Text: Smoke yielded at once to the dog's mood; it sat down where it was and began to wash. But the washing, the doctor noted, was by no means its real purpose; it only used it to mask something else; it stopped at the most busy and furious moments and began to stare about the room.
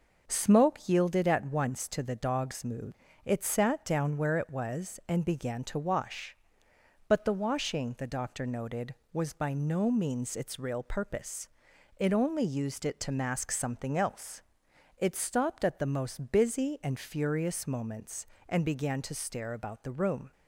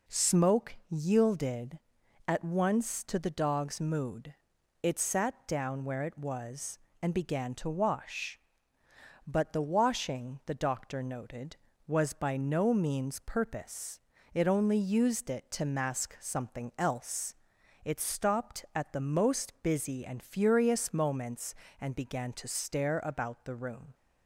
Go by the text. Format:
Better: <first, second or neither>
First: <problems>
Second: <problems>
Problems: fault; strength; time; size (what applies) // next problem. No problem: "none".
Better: first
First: none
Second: skips "its real"; at 13.2 s